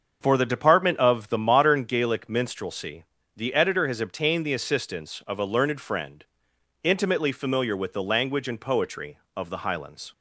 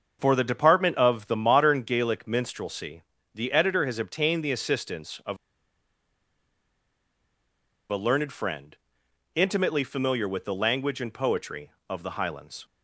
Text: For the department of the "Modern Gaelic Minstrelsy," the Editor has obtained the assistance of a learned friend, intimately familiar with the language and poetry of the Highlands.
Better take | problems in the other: first | starts louder than the rest; until 1.2 s; 6.5 dB; also in the first // pauses between "of" and "a"; strong; at 5.3 s; 2.5 s long

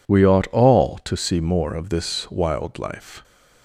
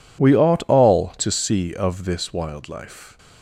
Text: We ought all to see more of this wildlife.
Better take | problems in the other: first | skips "more"; at 1.7 s

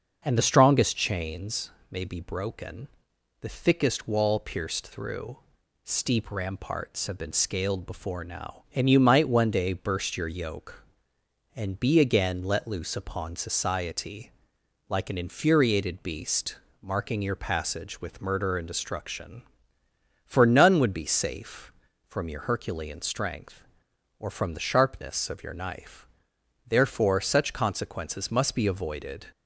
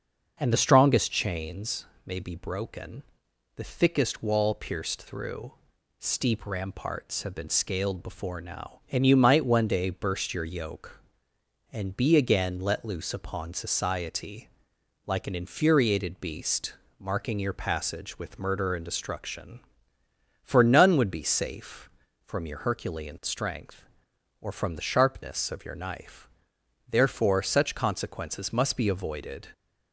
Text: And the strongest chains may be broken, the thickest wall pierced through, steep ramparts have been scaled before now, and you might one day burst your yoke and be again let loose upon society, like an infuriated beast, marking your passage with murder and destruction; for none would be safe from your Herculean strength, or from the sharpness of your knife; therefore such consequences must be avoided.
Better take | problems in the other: neither | starts louder than the rest; the same in both // pauses between "chains" and "may"; slight; the same in both

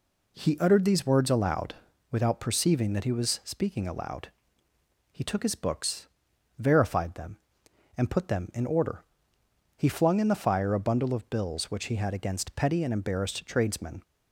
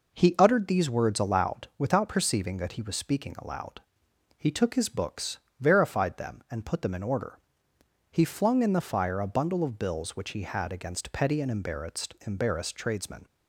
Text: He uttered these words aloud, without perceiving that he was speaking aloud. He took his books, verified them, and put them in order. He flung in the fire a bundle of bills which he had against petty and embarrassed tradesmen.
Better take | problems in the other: first | says "embarrassed" twice; at 12.2 s

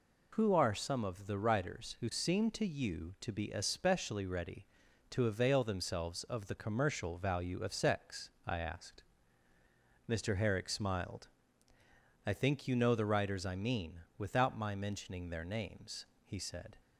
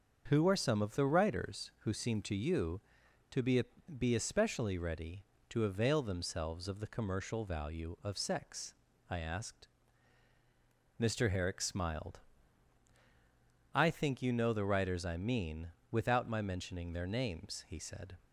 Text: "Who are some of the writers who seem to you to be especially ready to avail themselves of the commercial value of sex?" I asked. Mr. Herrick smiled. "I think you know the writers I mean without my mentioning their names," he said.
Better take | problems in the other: first | starts louder than the rest; until 1.2 s; 6.5 dB // says "be" twice; at 3.9 s // pauses between "mean" and "without"; slight; at 15.7 s; 0.18 s long; slight in the first

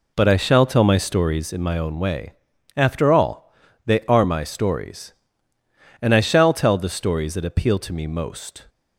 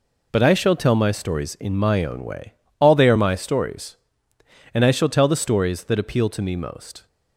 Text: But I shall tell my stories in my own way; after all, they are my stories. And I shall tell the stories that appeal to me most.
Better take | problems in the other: first | skips "after"; at 2.6 s

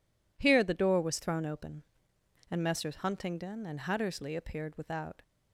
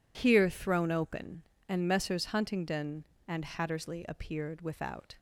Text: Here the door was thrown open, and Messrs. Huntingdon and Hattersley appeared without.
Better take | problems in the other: first | skips "the door was"; at 0.4 s

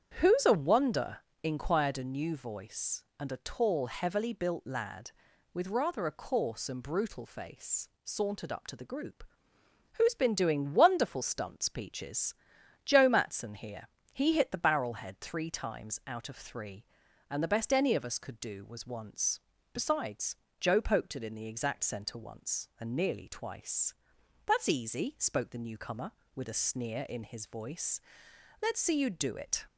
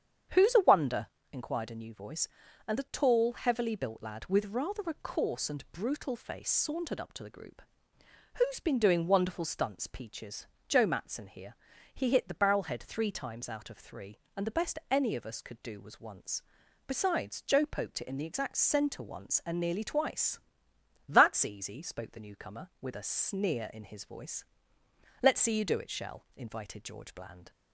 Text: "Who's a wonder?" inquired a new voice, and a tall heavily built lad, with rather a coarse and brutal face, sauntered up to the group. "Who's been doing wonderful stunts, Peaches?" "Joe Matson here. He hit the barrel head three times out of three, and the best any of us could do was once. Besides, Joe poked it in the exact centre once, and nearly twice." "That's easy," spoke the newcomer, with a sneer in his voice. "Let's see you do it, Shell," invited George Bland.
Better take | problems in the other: second | starts louder than the rest; strong; until 1.2 s; 8 dB; strong in the second // stops before "Shell invited George Bland"; at 29.6 s

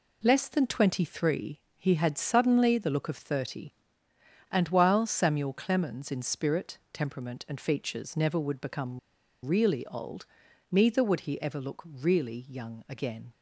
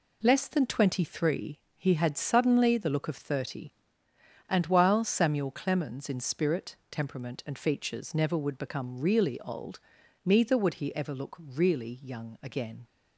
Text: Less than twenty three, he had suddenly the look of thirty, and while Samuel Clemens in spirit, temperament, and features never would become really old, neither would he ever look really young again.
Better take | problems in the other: second | pauses between "become" and "really"; at 8.9 s; 0.44 s long

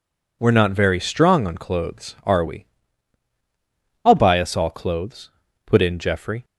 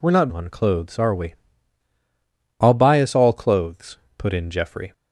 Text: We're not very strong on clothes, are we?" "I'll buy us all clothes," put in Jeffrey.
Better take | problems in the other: first | skips "very strong"; at 0.3 s

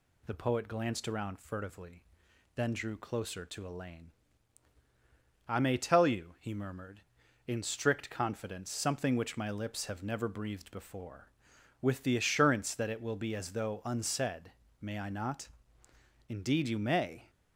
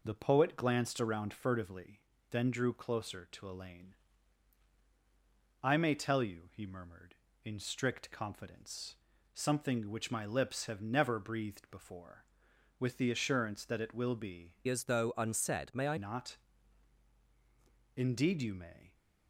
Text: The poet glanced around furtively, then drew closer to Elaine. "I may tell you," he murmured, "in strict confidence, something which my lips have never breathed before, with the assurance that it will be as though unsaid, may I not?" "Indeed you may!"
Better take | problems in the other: first | changes voice from "as" to "I"; from 14.6 to 15.9 s; 1.3 s long

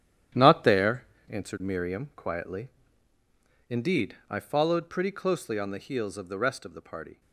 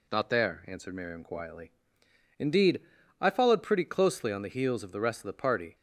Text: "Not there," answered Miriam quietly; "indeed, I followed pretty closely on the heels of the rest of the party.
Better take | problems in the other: second | gets quieter; strong; throughout; 11 dB

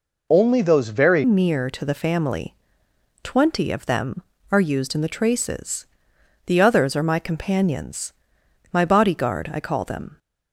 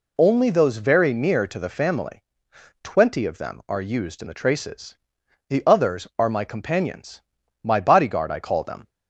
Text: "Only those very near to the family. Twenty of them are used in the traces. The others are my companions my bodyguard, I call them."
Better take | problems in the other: second | changes voice at "near"; from 1.2 s on; 8.9 s long // pauses between "companions" and "my"; noticeable; at 8.1 s; 0.58 s long; also in the second

